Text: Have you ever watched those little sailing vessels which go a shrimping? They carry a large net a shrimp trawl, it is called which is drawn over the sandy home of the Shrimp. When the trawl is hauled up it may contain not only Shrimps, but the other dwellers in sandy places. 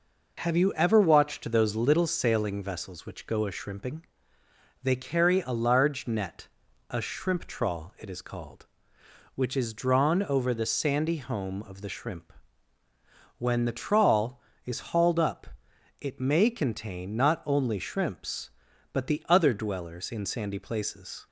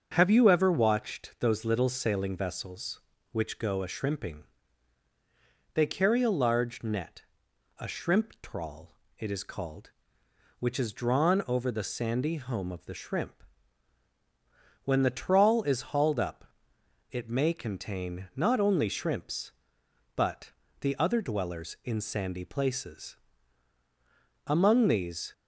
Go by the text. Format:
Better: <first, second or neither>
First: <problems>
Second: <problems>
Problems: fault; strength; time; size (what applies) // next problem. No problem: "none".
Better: first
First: pauses between "net" and "a"; at 6.4 s; 0.42 s long // pauses between "up" and "it"; noticeable; at 15.4 s; 0.54 s long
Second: starts louder than the rest; until 1.1 s; 6.5 dB // pauses between "net" and "a"; noticeable; at 7.2 s; 0.56 s long // pauses between "up" and "it"; noticeable; at 16.4 s; 0.66 s long // pauses between "but" and "the"; slight; at 20.5 s; 0.30 s long // goes on to say "Among these"; noticeable; from 24.4 s on; 0.88 s long